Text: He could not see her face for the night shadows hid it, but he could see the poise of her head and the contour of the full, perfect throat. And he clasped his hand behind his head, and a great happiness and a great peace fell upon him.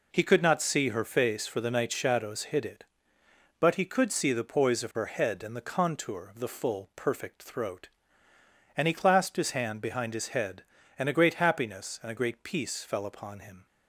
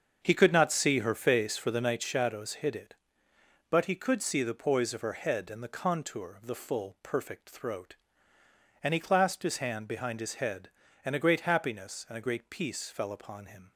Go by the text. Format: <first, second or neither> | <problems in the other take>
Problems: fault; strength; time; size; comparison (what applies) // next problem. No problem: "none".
first | starts louder than the rest; until 2.0 s; 6.5 dB